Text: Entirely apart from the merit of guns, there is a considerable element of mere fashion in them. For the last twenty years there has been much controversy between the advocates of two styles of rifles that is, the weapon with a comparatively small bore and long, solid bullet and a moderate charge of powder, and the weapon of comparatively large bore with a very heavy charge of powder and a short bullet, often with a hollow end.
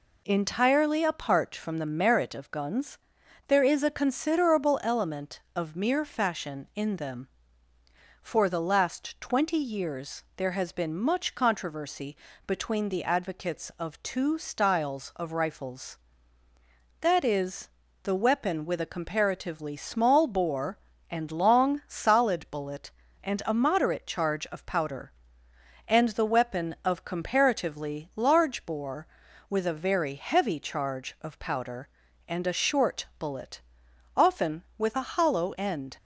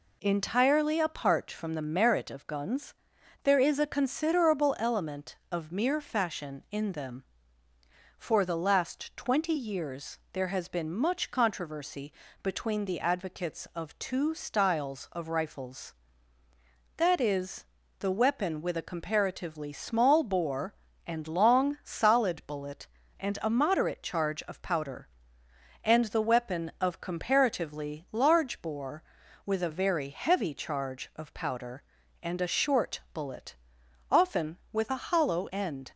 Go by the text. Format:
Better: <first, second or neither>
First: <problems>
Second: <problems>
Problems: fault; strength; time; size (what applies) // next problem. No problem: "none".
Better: neither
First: pauses between "controversy" and "between"; slight; at 12.1 s; 0.32 s long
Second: pauses between "controversy" and "between"; slight; at 12.1 s; 0.32 s long